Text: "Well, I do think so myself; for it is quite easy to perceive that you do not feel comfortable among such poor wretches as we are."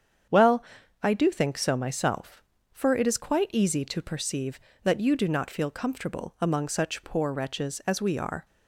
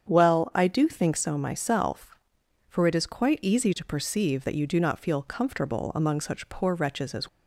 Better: first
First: starts louder than the rest; strong; until 1.7 s; 8 dB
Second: starts louder than the rest; strong; until 1.1 s; 8 dB // stops before "we are"; at 7.2 s

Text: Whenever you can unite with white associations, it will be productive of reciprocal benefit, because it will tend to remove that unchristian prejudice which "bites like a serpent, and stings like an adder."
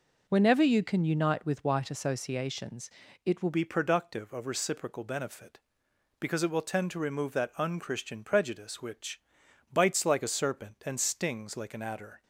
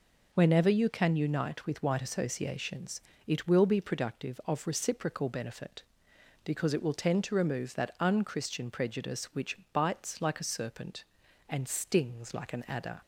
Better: second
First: changes voice at "be"; from 3.5 s on; 8.7 s long // pauses between "which" and "bites"; noticeable; at 9.1 s; 0.50 s long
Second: pauses between "which" and "bites"; slight; at 9.5 s; 0.16 s long

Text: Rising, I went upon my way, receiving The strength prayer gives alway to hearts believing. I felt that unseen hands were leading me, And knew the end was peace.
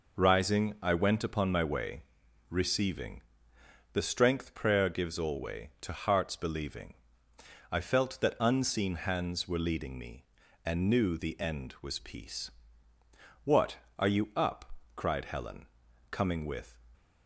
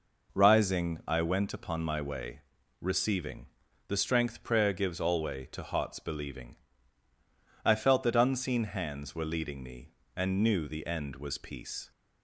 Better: second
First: pauses between "receiving" and "The"; noticeable; at 3.2 s; 0.72 s long // goes on to say "What are you up Cried Helen coming with"; strong; from 13.4 s on; 3.3 s long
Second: pauses between "receiving" and "The"; at 3.4 s; 0.42 s long

